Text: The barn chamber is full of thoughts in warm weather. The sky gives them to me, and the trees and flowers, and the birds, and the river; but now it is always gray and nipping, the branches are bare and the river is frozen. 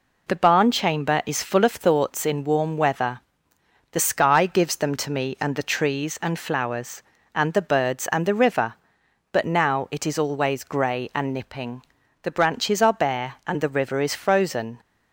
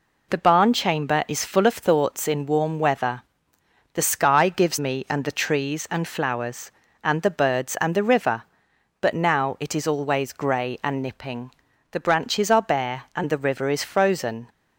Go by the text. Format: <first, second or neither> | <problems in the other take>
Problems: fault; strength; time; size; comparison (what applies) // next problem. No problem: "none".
first | skips "them to"; at 4.7 s